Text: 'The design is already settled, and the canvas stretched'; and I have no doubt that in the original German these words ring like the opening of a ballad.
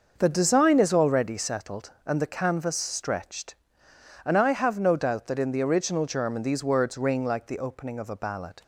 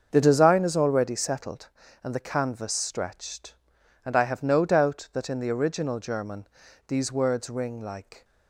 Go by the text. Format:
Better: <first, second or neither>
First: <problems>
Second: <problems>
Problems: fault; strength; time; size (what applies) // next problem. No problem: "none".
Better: first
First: starts louder than the rest; noticeable; until 1.1 s; 6 dB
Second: starts louder than the rest; until 1.1 s; 6.5 dB // pauses between "German" and "these"; at 6.4 s; 0.40 s long // stops before "the opening of a ballad"; at 8.2 s